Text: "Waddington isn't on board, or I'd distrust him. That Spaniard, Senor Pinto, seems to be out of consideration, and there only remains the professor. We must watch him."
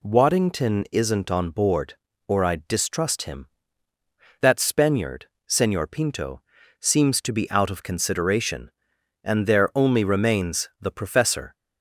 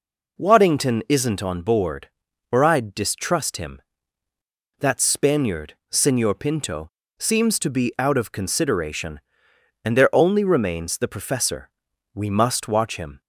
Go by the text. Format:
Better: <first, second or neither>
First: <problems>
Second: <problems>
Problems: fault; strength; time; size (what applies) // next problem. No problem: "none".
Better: second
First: stops before "We must watch him"; at 11.5 s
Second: none